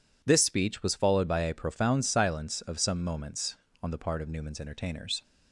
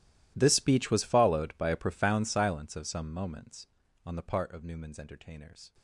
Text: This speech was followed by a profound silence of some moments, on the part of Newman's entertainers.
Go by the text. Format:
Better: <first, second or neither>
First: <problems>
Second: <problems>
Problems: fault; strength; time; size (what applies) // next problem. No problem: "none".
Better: first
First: none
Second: gets quieter; strong; throughout; 23.5 dB